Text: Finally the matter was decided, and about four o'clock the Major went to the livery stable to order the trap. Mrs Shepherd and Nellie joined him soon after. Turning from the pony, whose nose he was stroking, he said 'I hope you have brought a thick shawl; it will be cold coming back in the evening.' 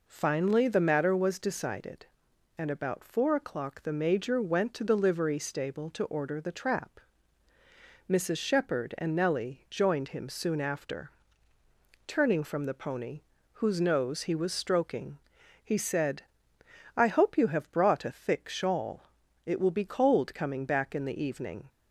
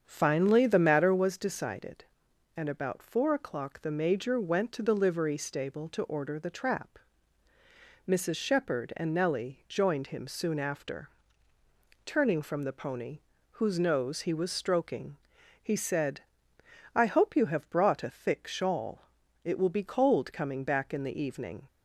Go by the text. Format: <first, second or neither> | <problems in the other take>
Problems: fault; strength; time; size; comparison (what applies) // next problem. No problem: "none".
first | starts louder than the rest; strong; until 1.3 s; 7.5 dB // pauses between "said" and "I"; noticeable; at 16.2 s; 0.74 s long; noticeable in the first